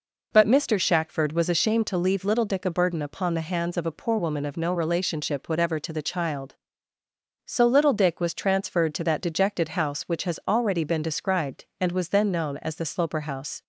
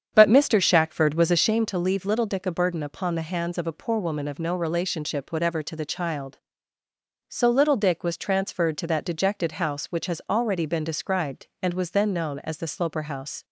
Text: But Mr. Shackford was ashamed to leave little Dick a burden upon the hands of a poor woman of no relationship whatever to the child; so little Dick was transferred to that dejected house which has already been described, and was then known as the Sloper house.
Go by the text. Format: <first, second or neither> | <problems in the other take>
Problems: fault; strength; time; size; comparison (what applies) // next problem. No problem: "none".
first | starts louder than the rest; strong; until 1.6 s; 8 dB